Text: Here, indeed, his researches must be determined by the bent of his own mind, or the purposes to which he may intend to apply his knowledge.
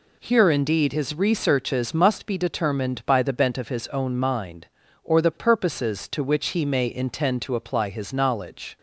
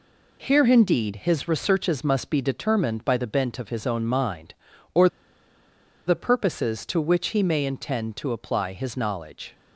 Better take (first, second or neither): first